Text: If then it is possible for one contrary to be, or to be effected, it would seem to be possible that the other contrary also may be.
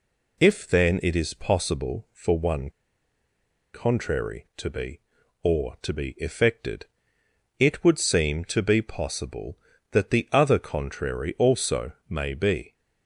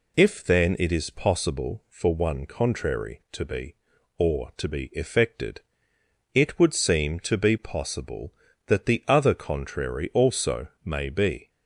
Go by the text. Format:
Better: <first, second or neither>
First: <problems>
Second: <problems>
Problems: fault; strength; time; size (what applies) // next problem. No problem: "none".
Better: second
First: pauses between "one" and "contrary"; at 2.6 s; 1.0 s long // pauses between "also" and "may"; slight; at 11.9 s; 0.16 s long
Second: pauses between "also" and "may"; slight; at 10.6 s; 0.16 s long